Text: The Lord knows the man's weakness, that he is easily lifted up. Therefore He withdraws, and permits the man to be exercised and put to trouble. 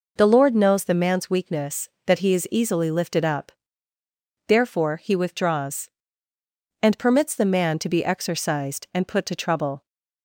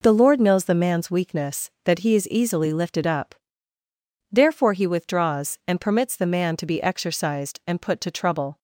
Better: neither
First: none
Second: none

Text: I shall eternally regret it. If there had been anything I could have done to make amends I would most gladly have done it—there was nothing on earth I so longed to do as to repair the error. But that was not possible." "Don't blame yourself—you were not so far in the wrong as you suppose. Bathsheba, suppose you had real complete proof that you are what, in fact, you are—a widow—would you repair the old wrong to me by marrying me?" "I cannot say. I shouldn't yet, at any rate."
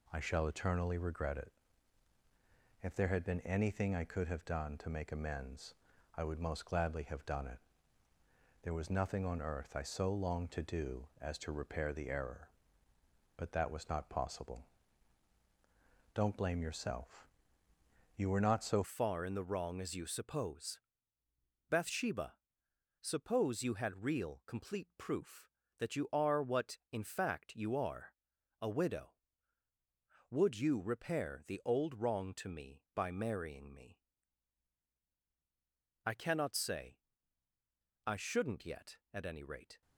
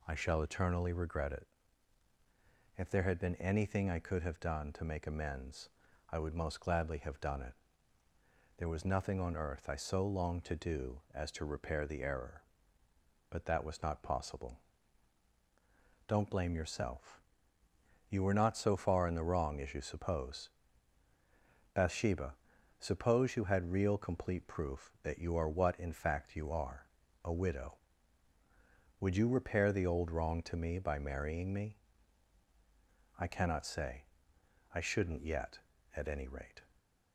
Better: second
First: pauses between "amends" and "I"; at 5.7 s; 0.42 s long // changes voice at "far"; from 18.8 s on; 21.0 s long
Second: pauses between "amends" and "I"; at 5.6 s; 0.42 s long

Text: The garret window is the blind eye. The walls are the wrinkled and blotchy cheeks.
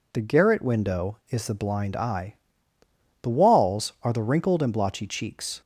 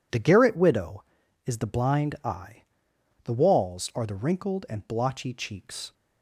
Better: first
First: none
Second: says "widow" for "window"; at 0.5 s

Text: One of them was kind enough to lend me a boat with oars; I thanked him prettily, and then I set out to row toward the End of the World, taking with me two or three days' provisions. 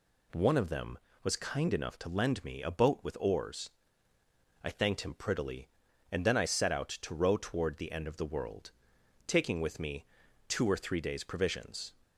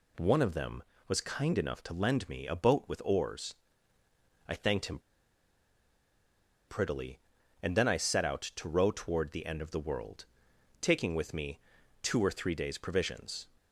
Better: first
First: pauses between "me" and "two"; at 10.0 s; 0.44 s long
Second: pauses between "him" and "prettily"; strong; at 4.9 s; 1.6 s long // pauses between "me" and "two"; at 11.5 s; 0.44 s long

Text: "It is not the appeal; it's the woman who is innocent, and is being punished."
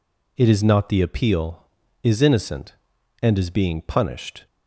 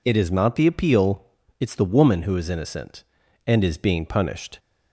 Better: second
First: skips "it's the woman who"; at 1.8 s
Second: none

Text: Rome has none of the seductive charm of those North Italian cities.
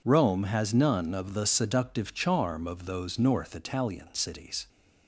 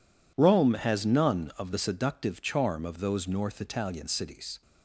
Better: neither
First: none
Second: none

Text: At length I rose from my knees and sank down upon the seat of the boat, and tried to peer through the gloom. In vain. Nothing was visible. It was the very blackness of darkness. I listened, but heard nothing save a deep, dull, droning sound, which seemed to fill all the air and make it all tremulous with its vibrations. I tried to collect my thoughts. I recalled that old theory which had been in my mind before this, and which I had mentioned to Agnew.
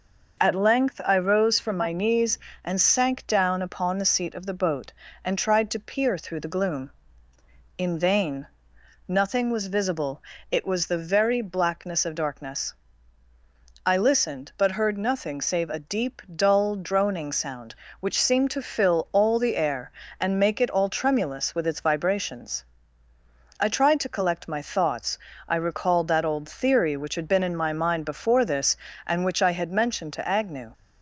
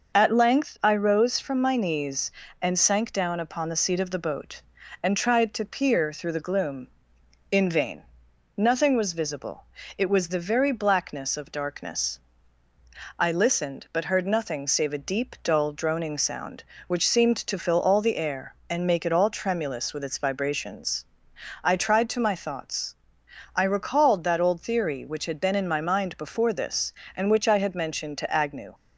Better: first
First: none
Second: skips "collect"; at 22.1 s

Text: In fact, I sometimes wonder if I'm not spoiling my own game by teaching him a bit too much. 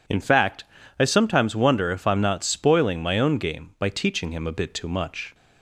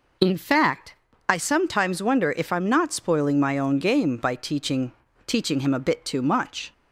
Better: first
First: none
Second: says "teaching" twice; at 5.2 s

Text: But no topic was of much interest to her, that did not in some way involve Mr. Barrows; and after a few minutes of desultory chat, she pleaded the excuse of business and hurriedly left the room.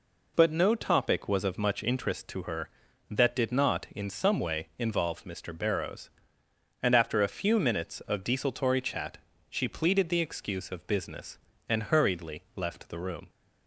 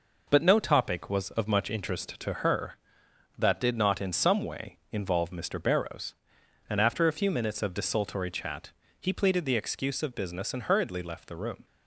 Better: first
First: none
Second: says "he" for "she"; at 8.9 s

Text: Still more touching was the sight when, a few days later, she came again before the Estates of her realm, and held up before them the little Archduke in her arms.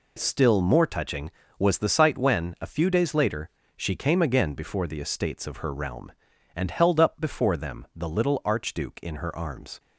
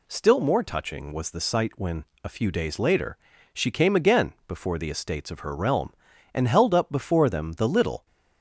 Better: first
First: none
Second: stops before "Archduke in her arms"; at 8.0 s

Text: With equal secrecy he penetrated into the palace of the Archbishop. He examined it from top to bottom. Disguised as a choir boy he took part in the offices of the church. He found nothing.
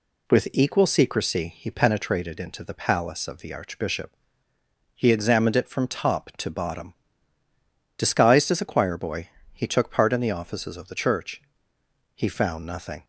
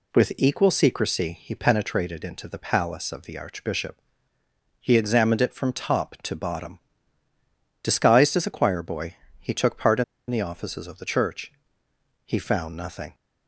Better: first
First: pauses between "boy" and "he"; slight; at 9.2 s; 0.24 s long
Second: pauses between "boy" and "he"; slight; at 9.1 s; 0.24 s long // pauses between "in" and "the"; slight; at 10.0 s; 0.25 s long

